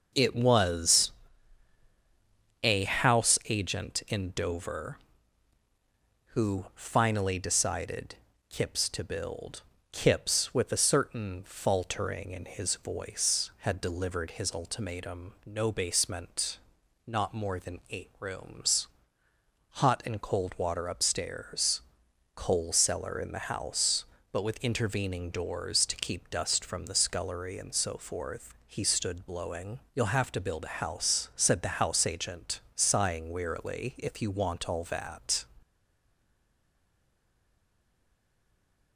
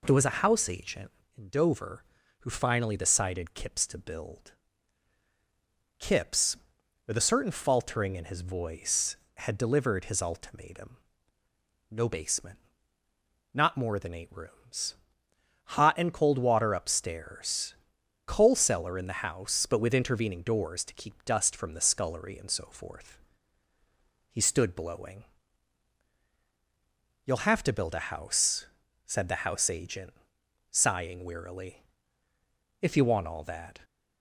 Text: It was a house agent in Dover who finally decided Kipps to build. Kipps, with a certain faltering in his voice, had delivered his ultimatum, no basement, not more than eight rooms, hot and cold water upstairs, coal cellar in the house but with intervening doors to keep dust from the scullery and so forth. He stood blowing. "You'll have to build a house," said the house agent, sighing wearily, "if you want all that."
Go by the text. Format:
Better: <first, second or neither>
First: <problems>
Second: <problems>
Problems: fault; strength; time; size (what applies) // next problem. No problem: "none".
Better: second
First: pauses between "was" and "a"; strong; at 1.0 s; 1.5 s long // pauses between "decided" and "Kipps"; slight; at 8.1 s; 0.34 s long // stays silent after the last word; strong; from 35.6 s on; 3.3 s long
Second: none